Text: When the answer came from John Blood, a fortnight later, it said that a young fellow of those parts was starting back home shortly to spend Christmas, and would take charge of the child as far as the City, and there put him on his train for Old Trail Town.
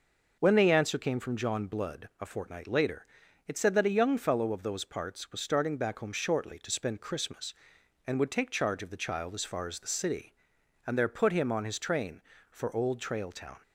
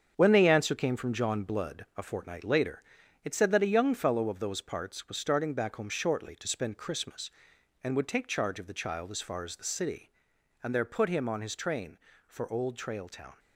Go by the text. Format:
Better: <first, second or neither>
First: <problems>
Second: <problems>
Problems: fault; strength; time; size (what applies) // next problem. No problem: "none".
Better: first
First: none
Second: gets quieter; strong; throughout; 7 dB